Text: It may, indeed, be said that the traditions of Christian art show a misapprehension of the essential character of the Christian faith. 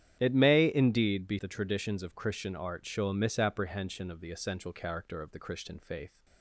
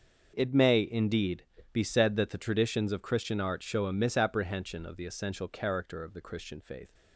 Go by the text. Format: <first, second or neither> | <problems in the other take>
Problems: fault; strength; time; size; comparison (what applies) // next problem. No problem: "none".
second | starts louder than the rest; strong; until 1.2 s; 10 dB; noticeable in the second // skips "said that"; at 1.3 s